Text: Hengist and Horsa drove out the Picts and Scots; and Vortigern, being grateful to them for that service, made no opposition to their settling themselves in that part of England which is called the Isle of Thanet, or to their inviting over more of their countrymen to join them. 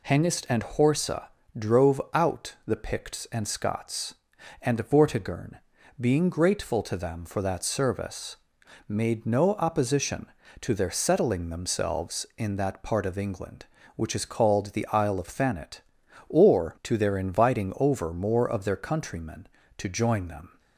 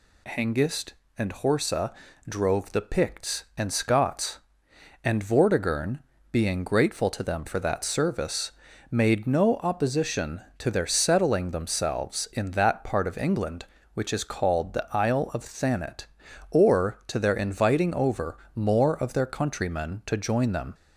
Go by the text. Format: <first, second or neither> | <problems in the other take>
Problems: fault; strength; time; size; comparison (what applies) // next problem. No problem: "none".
first | pauses between "Horsa" and "drove"; slight; at 1.9 s; 0.36 s long; slight in the first // skips "out"; at 2.7 s // pauses between "over" and "more"; slight; at 18.3 s; 0.18 s long